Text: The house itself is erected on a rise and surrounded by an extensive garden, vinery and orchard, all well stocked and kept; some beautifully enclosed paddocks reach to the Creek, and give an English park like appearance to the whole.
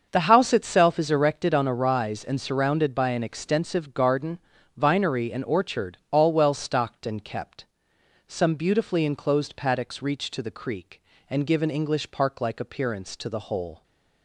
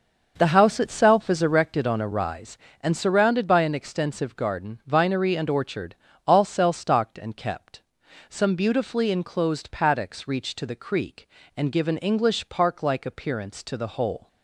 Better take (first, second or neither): first